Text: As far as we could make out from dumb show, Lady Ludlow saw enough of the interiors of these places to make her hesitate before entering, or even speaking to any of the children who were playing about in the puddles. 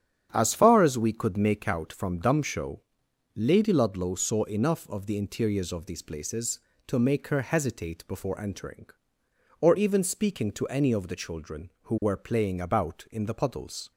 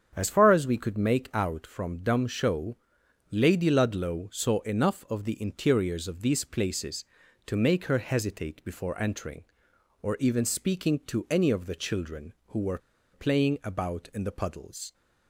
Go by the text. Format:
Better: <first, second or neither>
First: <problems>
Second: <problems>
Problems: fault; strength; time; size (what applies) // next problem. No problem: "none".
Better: first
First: starts louder than the rest; strong; until 1.3 s; 9 dB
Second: starts louder than the rest; strong; until 1.1 s; 8 dB // pauses between "were" and "playing"; slight; at 12.7 s; 0.35 s long